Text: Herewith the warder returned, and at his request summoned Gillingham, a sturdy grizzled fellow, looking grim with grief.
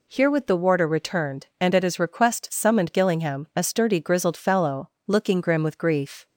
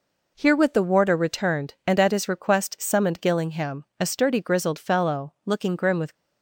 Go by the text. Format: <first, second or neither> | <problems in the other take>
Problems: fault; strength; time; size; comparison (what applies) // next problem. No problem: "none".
first | stops before "grief"; at 6.1 s